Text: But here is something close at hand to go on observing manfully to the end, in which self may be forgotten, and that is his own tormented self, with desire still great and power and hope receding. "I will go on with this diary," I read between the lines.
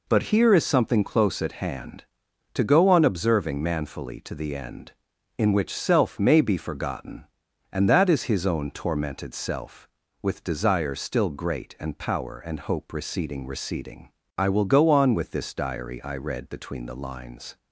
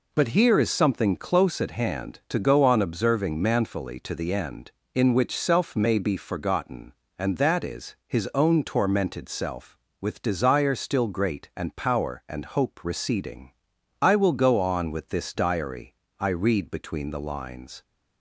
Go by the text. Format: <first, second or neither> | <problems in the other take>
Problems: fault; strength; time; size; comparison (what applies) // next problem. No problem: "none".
second | says "receding" twice; at 13.4 s